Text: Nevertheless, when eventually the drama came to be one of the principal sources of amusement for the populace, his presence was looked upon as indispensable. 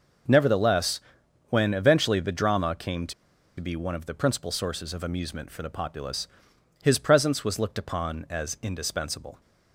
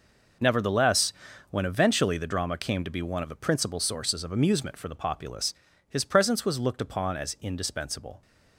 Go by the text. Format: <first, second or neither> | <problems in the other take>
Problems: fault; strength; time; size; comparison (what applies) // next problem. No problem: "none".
second | pauses between "to" and "be"; noticeable; at 3.1 s; 0.46 s long